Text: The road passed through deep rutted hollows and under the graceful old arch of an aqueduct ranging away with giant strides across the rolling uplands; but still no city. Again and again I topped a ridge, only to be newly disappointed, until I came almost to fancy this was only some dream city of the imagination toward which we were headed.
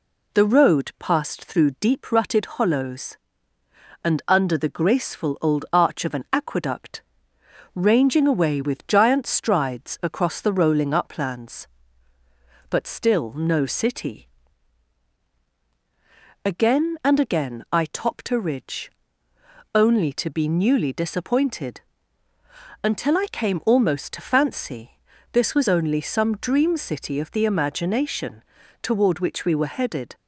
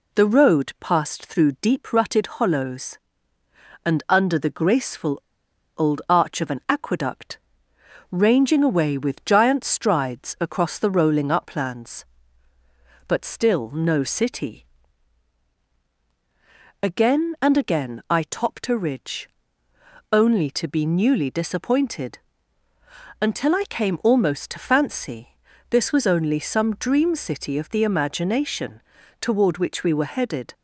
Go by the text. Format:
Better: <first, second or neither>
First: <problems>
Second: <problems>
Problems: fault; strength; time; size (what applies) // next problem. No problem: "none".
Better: first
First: pauses between "aqueduct" and "ranging"; noticeable; at 7.0 s; 0.74 s long // pauses between "fancy" and "this"; at 24.9 s; 0.40 s long // pauses between "imagination" and "toward"; at 28.4 s; 0.38 s long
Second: pauses between "graceful" and "old"; noticeable; at 5.1 s; 0.59 s long // pauses between "aqueduct" and "ranging"; noticeable; at 7.3 s; 0.74 s long // pauses between "fancy" and "this"; at 25.2 s; 0.40 s long // pauses between "imagination" and "toward"; at 28.8 s; 0.38 s long